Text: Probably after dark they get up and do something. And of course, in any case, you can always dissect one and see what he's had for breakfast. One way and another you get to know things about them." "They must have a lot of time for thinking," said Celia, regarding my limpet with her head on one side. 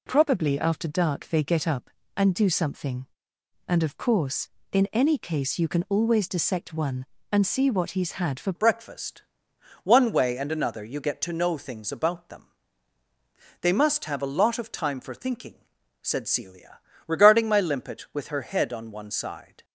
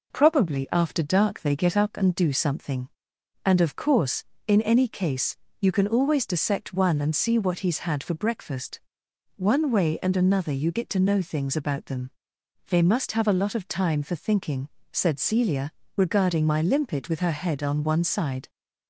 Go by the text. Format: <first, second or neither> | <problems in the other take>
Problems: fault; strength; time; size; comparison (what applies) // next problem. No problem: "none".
second | changes voice at "breakfast"; from 8.5 s on; 11.1 s long